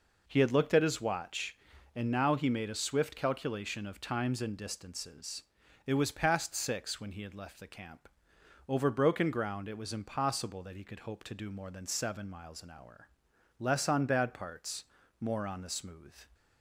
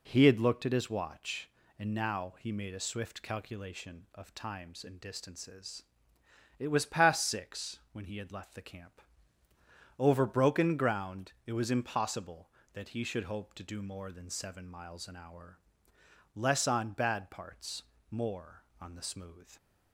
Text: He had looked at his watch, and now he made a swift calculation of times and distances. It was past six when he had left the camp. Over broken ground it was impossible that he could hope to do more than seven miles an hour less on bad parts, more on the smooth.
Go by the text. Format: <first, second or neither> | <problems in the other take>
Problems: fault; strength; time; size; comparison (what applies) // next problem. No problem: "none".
first | says "should" for "could"; at 13.0 s // pauses between "hour" and "less"; noticeable; at 15.5 s; 0.78 s long; noticeable in the first